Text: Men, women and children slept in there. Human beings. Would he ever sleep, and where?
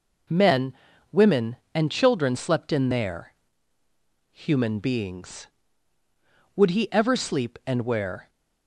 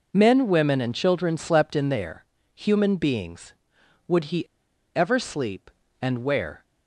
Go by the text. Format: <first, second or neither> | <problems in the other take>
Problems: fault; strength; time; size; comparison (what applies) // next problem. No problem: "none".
first | pauses between "he" and "ever"; noticeable; at 4.4 s; 0.48 s long